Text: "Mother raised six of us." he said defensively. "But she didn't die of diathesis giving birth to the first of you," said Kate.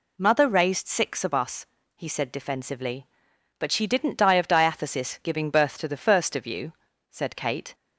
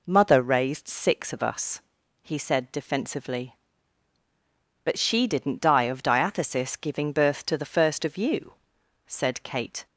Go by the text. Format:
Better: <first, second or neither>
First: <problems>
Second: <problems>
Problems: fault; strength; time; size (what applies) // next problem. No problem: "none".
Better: neither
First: none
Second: none